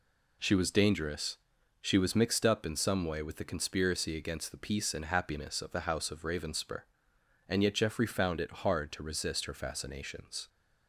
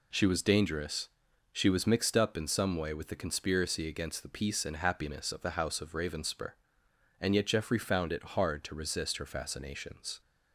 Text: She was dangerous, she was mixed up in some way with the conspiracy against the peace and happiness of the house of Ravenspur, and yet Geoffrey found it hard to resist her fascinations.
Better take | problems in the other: neither | none

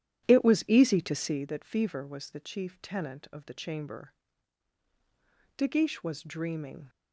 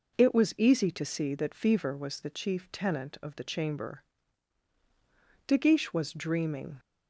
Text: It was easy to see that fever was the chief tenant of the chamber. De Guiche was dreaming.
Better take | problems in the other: second | starts louder than the rest; strong; until 1.5 s; 11 dB

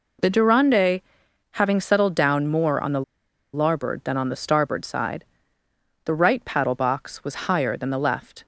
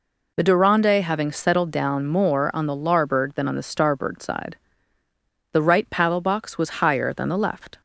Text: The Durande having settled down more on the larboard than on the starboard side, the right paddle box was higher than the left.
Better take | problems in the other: second | pauses between "Durande" and "having"; noticeable; at 0.9 s; 0.52 s long // pauses between "the" and "larboard"; noticeable; at 3.0 s; 0.51 s long

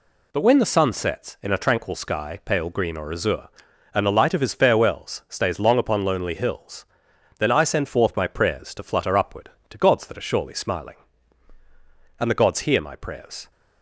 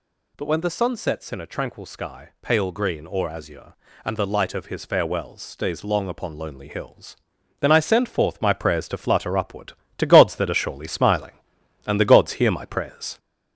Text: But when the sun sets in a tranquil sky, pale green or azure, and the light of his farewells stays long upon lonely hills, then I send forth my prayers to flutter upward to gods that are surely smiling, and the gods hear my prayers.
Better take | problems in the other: first | gets louder; throughout; 4 dB

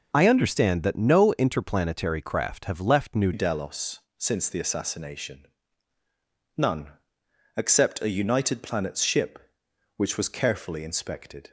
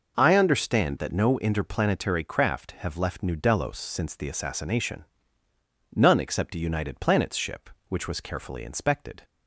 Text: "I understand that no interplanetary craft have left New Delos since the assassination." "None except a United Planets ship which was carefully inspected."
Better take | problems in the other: second | changes voice at "Delos"; from 3.3 s on; 8.2 s long // pauses between "Delos" and "since"; slight; at 4.0 s; 0.18 s long // pauses between "None" and "except"; noticeable; at 6.9 s; 0.64 s long

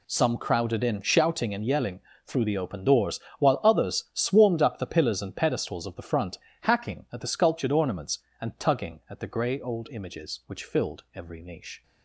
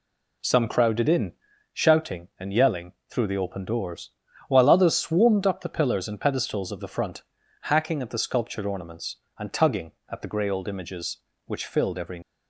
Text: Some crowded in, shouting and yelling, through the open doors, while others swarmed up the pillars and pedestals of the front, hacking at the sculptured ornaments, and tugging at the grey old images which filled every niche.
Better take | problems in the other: first | stops before "niche"; at 12.2 s

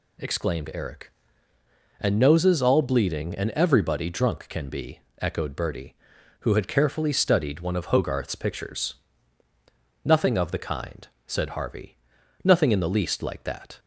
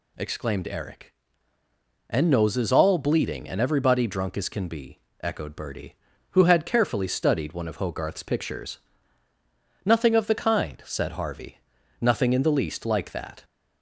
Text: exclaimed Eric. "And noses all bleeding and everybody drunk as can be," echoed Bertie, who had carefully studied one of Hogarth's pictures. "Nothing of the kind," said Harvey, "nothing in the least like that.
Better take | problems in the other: second | skips "as"; at 4.4 s

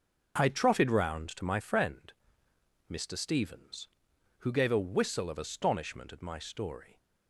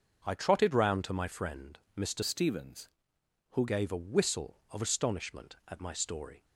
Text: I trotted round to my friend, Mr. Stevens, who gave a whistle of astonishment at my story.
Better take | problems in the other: first | starts louder than the rest; until 1.2 s; 6.5 dB; also in the first // changes voice from "Stevens" to "who"; from 2.2 to 3.6 s; 1.4 s long

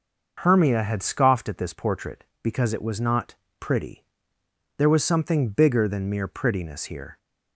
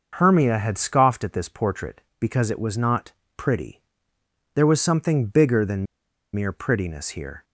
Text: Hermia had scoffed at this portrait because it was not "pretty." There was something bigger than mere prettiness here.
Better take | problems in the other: first | starts louder than the rest; noticeable; until 1.1 s; 6 dB // pauses between "not" and "pretty"; slight; at 3.0 s; 0.26 s long; slight in the first // pauses between "than" and "mere"; noticeable; at 5.8 s; 0.49 s long

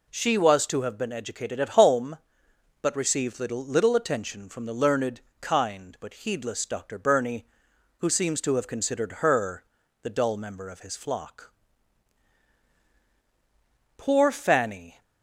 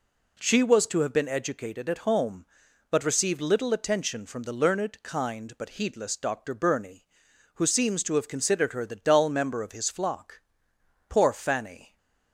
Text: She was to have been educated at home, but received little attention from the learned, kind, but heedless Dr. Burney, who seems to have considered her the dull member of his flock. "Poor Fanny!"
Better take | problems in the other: second | says "little" twice; at 3.6 s // pauses between "her" and "the"; at 9.6 s; 0.38 s long

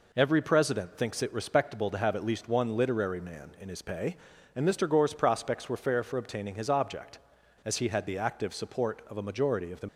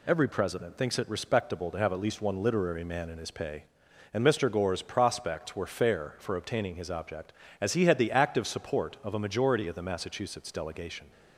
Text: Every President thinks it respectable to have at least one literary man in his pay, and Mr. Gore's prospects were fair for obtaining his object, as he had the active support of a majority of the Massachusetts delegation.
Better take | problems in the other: second | stops before "Massachusetts delegation"; at 9.8 s

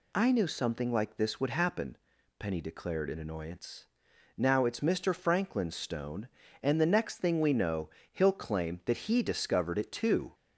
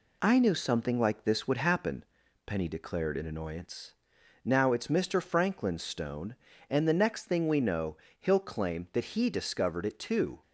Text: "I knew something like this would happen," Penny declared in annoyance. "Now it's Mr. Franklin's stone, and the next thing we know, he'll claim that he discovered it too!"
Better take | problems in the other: first | gets quieter; slight; throughout; 3 dB

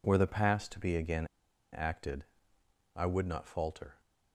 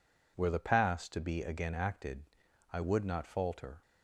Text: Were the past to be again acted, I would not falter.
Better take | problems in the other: second | pauses between "again" and "acted"; noticeable; at 1.2 s; 0.47 s long

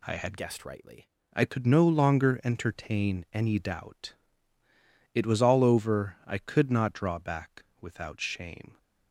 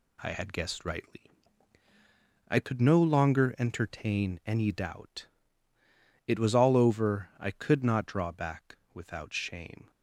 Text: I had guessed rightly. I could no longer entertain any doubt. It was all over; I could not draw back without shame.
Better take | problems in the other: second | changes voice from "guessed" to "rightly"; from 0.3 to 1.0 s; 0.7 s long // pauses between "back" and "without"; slight; at 7.6 s; 0.18 s long; slight in the second

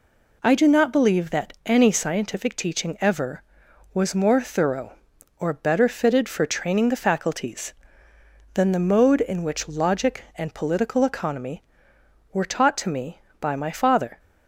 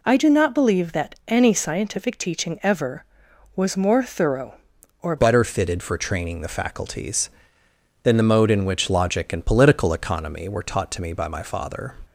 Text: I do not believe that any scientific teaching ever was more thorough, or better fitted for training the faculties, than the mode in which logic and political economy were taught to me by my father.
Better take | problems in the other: first | changes voice at "better"; from 5.1 s on; 6.8 s long

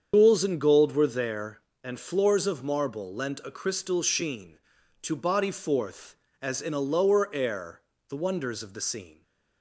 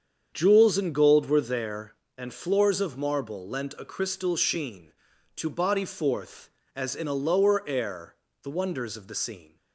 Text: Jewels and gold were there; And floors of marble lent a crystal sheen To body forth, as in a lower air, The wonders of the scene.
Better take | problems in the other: second | loses the start of "Jewels"; at 0.1 s; 135 ms // starts louder than the rest; strong; until 1.1 s; 7.5 dB; strong in the second

